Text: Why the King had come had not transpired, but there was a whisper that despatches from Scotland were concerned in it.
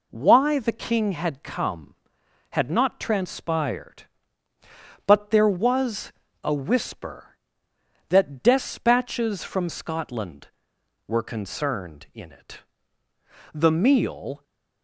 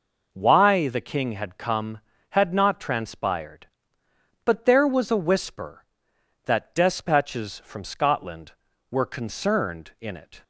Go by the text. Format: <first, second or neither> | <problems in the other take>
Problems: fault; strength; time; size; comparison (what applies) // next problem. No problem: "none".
second | pauses between "was" and "a"; slight; at 6.1 s; 0.32 s long // goes on to say "The meal"; noticeable; from 13.5 s on; 0.90 s long